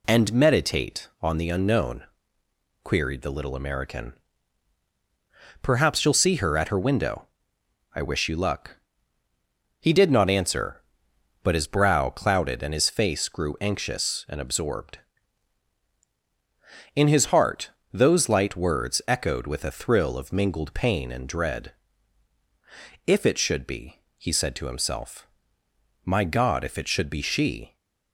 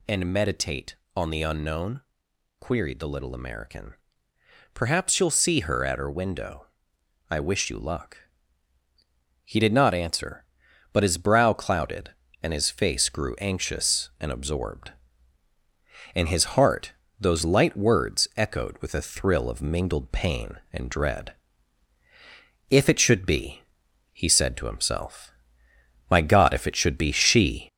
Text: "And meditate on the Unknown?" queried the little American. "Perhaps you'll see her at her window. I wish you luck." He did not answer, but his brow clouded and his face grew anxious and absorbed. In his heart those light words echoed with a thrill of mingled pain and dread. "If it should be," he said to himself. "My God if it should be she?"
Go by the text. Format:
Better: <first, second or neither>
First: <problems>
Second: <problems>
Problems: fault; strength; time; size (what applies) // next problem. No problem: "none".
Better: first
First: pauses between "heart" and "those"; slight; at 17.7 s; 0.20 s long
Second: gets louder; slight; throughout; 3 dB // pauses between "heart" and "those"; slight; at 16.9 s; 0.26 s long